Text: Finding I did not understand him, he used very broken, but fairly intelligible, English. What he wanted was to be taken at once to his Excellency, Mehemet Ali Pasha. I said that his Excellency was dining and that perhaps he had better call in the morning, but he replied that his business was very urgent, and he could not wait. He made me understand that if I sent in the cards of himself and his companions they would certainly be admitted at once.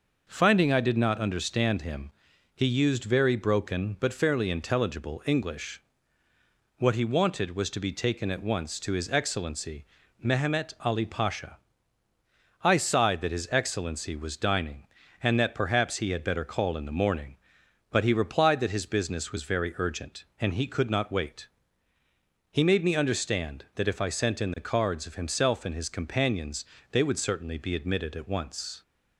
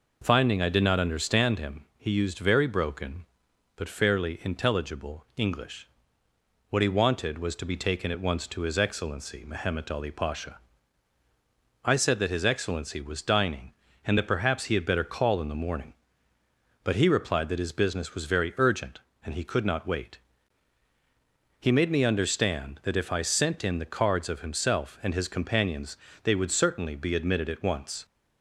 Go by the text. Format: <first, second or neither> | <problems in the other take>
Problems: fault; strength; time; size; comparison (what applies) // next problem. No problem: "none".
second | says "sighed" for "said"; at 12.7 s // pauses between "companions" and "they"; slight; at 26.6 s; 0.28 s long; slight in the second